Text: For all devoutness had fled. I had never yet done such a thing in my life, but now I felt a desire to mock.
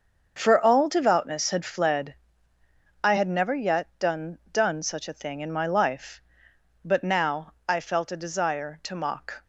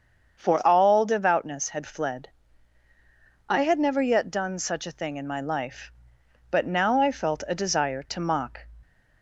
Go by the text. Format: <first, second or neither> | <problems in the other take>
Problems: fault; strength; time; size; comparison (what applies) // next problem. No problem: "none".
second | starts louder than the rest; until 1.3 s; 6.5 dB; also in the second // says "done" twice; at 4.5 s // pauses between "now" and "I"; slight; at 7.5 s; 0.16 s long